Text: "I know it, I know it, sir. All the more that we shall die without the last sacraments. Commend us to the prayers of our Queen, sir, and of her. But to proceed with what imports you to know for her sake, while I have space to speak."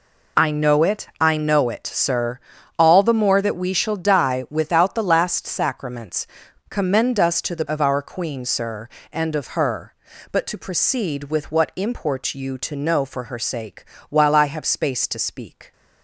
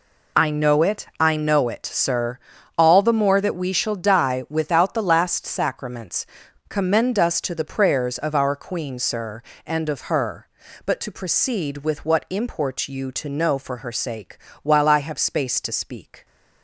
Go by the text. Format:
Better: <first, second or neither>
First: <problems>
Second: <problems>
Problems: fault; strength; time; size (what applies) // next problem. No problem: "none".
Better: second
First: skips "prayers"; at 7.6 s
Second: none